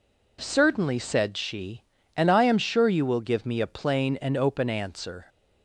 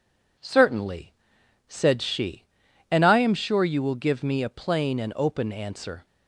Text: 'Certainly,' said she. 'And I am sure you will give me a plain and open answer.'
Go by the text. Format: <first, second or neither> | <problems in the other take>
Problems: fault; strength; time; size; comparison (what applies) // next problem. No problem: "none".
neither | none